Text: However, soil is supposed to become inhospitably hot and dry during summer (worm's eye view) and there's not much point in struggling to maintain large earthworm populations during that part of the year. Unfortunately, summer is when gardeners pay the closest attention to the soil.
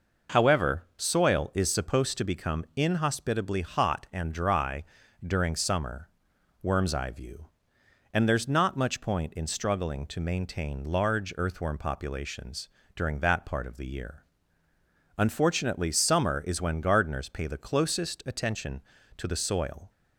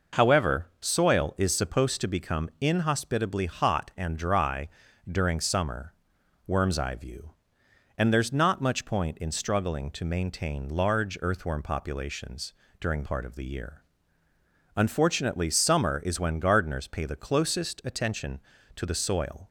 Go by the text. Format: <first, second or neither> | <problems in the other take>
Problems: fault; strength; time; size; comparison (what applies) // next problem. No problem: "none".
first | pauses between "dry" and "during"; at 4.6 s; 0.42 s long; also in the first // pauses between "populations" and "during"; slight; at 12.5 s; 0.26 s long; slight in the first // skips "that"; at 13.0 s